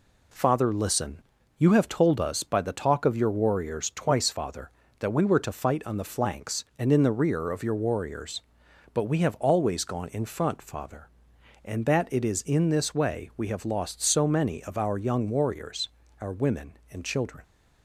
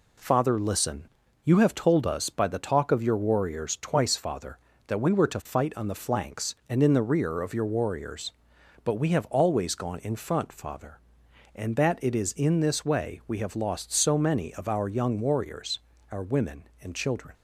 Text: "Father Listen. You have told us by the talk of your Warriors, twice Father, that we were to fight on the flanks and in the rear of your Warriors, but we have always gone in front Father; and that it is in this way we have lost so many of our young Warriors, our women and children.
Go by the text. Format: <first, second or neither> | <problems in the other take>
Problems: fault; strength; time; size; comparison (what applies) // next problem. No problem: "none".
neither | none